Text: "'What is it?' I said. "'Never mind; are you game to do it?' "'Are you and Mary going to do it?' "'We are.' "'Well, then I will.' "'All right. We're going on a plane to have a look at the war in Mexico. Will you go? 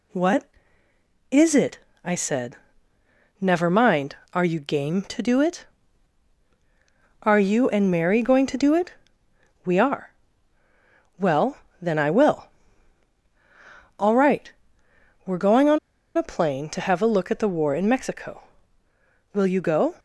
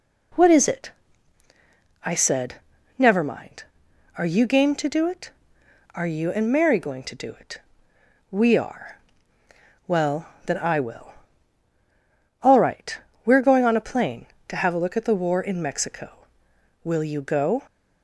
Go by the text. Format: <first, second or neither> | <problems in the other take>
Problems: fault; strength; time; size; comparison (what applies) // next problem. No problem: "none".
second | pauses between "on" and "a"; at 15.7 s; 0.37 s long